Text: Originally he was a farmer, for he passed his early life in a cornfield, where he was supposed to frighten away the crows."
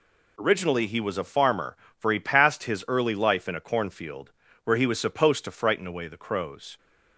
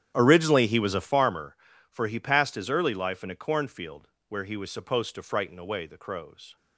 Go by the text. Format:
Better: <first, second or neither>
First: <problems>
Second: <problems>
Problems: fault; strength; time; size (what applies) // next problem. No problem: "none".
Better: first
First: none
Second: starts louder than the rest; strong; until 1.3 s; 10 dB